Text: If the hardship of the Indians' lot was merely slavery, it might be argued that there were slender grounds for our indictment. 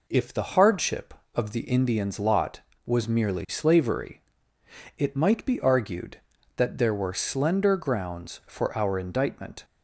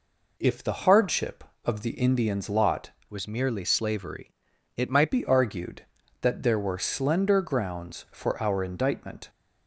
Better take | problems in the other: first | changes voice from "was" to "might"; from 3.0 to 5.1 s; 2.1 s long

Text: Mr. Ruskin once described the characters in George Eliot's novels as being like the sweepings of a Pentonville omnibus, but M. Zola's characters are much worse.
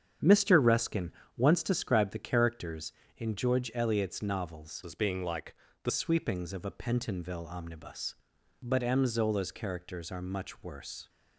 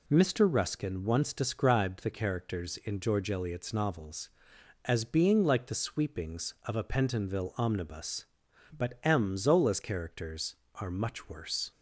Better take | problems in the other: second | starts louder than the rest; strong; until 1.4 s; 8 dB // pauses between "Ruskin" and "once"; slight; at 1.1 s; 0.26 s long // changes voice from "as" to "the"; from 4.8 to 5.9 s; 1.1 s long // pauses between "like" and "the"; slight; at 5.5 s; 0.30 s long

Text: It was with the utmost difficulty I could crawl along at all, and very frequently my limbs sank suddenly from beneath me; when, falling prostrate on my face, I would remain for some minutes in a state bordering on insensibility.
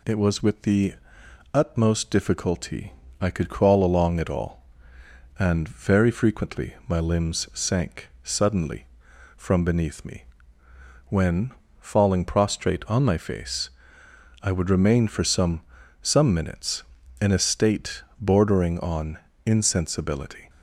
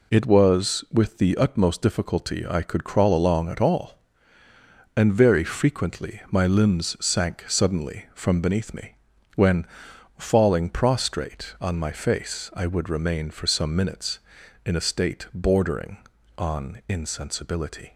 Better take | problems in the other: second | pauses between "the" and "utmost"; noticeable; at 0.9 s; 0.58 s long // pauses between "difficulty" and "I"; slight; at 2.9 s; 0.26 s long // says "some" twice; at 16.0 s // pauses between "state" and "bordering"; slight; at 18.0 s; 0.18 s long // pauses between "on" and "insensibility"; slight; at 19.1 s; 0.26 s long

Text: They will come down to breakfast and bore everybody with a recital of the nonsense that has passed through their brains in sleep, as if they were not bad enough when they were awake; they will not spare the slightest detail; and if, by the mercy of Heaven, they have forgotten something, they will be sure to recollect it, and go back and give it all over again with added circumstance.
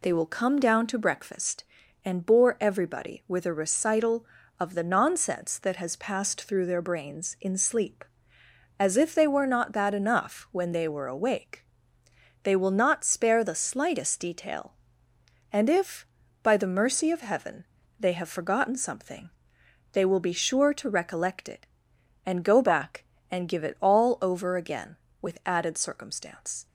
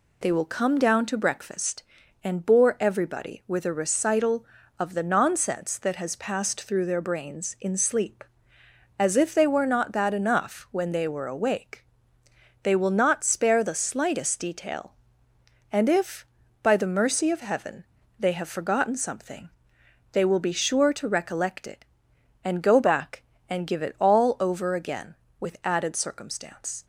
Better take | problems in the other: neither | none

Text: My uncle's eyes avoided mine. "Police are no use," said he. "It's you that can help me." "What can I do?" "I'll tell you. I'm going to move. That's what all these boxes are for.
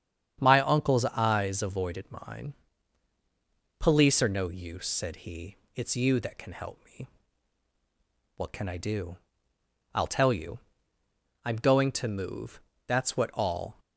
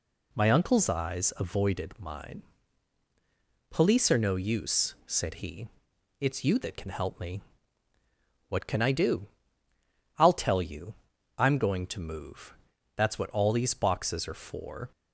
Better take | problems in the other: second | starts louder than the rest; strong; until 1.4 s; 8.5 dB // stops before "these boxes are for"; at 13.7 s

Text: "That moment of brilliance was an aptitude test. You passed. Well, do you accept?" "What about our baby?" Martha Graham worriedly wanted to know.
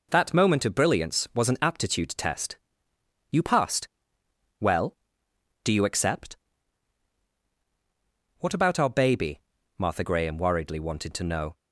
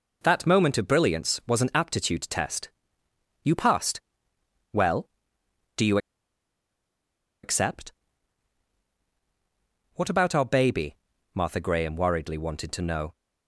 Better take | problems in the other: first | pauses between "you" and "accept"; strong; at 5.9 s; 1.4 s long

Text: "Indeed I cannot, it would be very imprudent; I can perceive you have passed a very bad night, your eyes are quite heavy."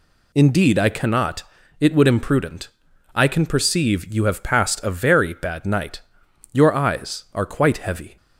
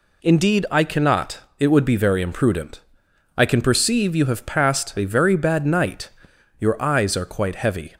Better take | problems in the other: second | skips "be very"; at 2.0 s

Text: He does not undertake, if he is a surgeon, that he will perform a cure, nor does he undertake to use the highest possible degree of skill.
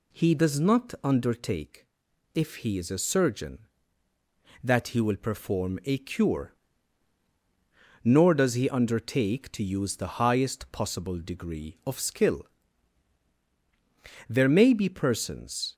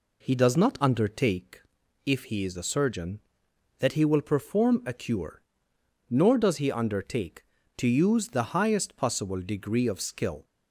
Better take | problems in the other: second | goes on to say "There may be persons"; from 14.2 s on; 1.4 s long

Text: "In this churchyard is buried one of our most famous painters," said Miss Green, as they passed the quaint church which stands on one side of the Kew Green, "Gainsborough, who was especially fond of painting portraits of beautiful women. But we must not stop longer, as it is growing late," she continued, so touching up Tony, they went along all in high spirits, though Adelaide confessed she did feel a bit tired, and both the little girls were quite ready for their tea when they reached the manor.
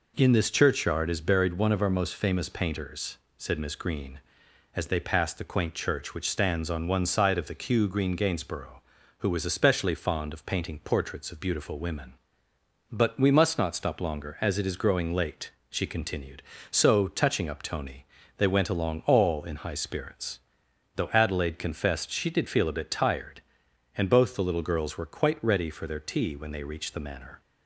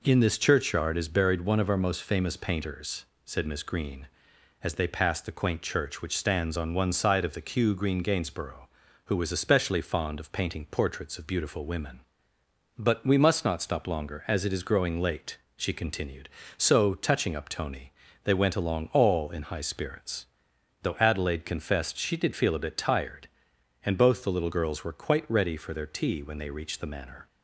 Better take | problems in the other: neither | none

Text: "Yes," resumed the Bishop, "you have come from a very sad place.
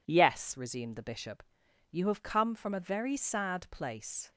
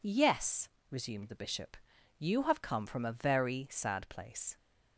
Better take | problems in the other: neither | none

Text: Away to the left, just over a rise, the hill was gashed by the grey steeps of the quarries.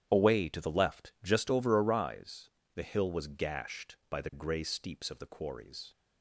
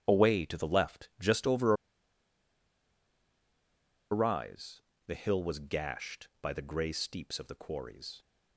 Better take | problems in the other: first | starts louder than the rest; strong; until 1.0 s; 9.5 dB; strong in the first // pauses between "over" and "a"; strong; at 1.7 s; 2.3 s long

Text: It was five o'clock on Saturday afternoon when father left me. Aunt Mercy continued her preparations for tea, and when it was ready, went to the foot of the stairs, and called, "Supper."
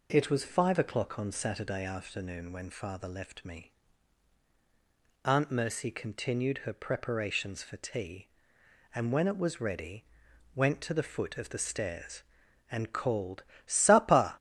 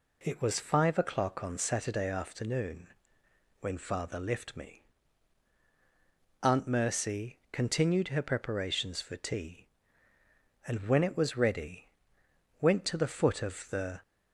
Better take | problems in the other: first | pauses between "afternoon" and "when"; noticeable; at 2.8 s; 0.72 s long // stops before "stairs and called Supper"; at 14.0 s

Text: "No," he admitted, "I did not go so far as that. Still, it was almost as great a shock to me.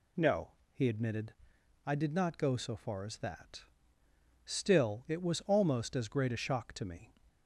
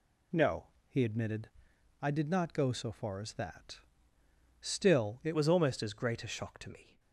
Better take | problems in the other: first | changes voice at "was"; from 5.3 s on; 1.6 s long

